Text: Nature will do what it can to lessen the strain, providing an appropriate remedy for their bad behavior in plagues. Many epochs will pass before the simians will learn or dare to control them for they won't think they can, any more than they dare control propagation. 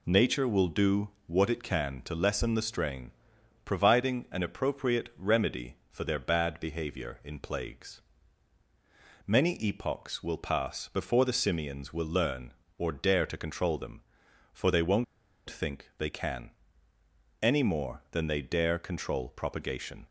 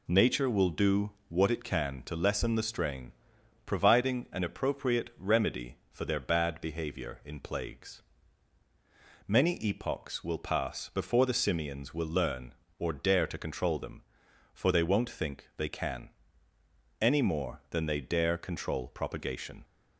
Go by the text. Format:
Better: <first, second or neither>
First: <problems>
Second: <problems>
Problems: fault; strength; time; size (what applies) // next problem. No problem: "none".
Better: second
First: pauses between "do" and "what"; slight; at 1.0 s; 0.20 s long // pauses between "won't" and "think"; at 15.0 s; 0.44 s long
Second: pauses between "do" and "what"; slight; at 1.0 s; 0.20 s long